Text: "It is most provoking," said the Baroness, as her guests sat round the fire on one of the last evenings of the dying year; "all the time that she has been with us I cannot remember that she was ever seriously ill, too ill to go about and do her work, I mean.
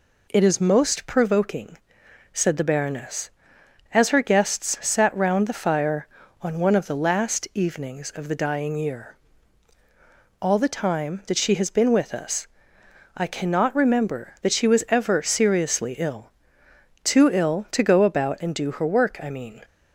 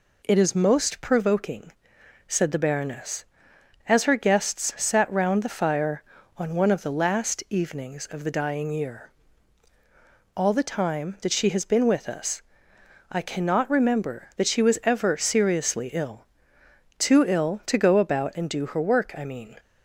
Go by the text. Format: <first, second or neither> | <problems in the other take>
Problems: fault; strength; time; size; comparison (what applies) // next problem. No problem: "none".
neither | pauses between "us" and "I"; noticeable; the same in both